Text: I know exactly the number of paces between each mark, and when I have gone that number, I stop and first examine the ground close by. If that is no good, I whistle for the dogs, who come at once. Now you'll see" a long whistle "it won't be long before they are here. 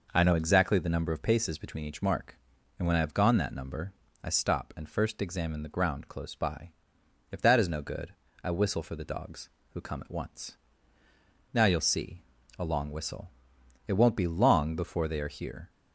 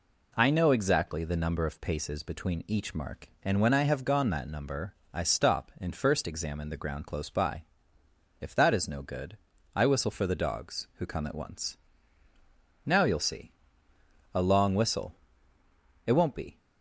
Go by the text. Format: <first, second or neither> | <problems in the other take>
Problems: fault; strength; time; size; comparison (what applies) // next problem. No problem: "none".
first | pauses between "see" and "a"; noticeable; at 13.5 s; 0.82 s long; slight in the first // pauses between "whistle" and "it"; noticeable; at 15.1 s; 0.94 s long; noticeable in the first // stops before "long before they are here"; at 16.5 s